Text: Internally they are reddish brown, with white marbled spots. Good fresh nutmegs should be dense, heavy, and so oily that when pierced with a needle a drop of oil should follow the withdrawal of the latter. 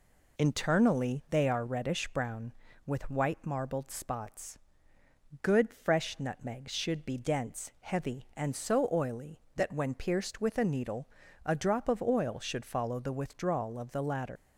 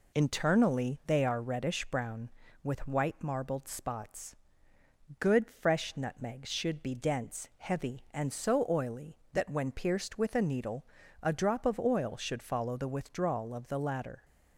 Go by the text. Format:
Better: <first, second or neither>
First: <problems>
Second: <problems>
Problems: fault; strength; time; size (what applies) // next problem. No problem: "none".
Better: second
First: pauses between "needle" and "a"; at 11.0 s; 0.38 s long // leaves "latter" unfinished; at 14.3 s; 125 ms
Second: pauses between "needle" and "a"; at 10.8 s; 0.38 s long